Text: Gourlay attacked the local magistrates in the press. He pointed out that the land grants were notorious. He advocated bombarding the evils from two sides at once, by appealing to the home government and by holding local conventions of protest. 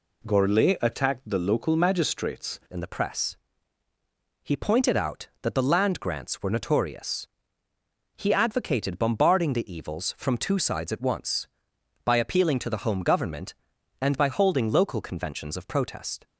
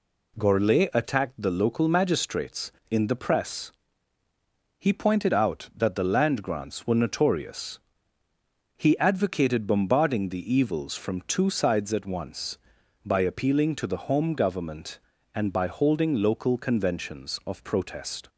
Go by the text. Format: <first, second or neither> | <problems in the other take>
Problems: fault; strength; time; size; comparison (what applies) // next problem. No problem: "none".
second | changes voice at "in"; from 2.7 s on; 13.5 s long